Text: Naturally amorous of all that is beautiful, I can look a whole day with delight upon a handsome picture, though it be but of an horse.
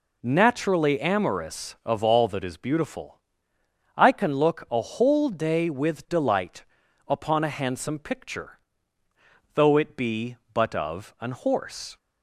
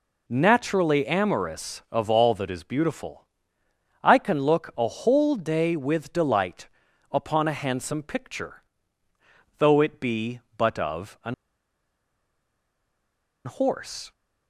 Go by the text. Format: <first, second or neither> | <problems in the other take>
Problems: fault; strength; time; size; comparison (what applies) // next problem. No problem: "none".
first | pauses between "delight" and "upon"; at 6.6 s; 0.44 s long; also in the first // pauses between "an" and "horse"; strong; at 11.3 s; 2.1 s long